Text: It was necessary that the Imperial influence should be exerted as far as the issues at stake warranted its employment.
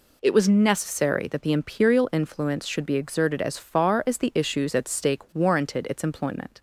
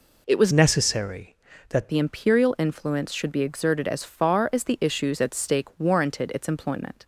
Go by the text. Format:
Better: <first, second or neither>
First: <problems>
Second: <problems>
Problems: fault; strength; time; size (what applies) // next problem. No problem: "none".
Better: first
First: none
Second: changes voice from "necessary" to "that"; from 0.5 to 1.8 s; 1.3 s long